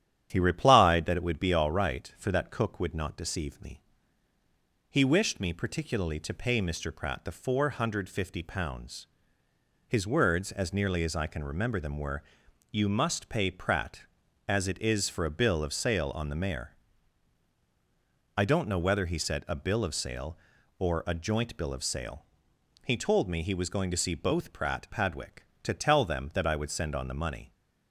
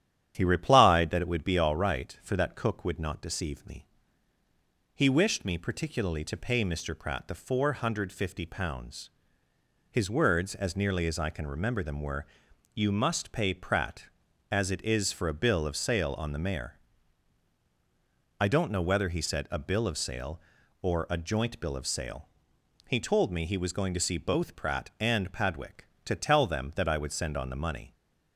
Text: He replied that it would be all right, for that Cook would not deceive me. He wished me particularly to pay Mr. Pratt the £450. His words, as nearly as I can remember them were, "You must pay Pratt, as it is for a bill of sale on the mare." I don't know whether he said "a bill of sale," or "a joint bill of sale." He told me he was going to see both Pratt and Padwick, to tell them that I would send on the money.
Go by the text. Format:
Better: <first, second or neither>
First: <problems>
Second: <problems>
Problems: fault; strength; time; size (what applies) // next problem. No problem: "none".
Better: second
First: starts louder than the rest; strong; until 1.3 s; 10 dB // skips "and"; at 24.8 s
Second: starts louder than the rest; strong; until 1.3 s; 10 dB